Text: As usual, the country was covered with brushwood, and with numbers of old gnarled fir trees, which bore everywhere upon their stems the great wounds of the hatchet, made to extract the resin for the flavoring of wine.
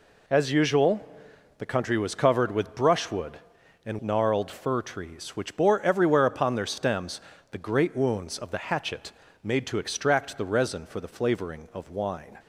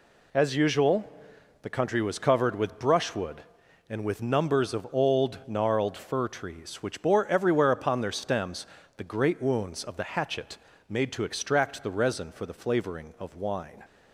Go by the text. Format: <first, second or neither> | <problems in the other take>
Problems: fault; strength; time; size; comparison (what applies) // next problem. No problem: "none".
second | skips "with numbers of old"; at 4.0 s // pauses between "stems" and "the"; slight; at 7.2 s; 0.30 s long; slight in the second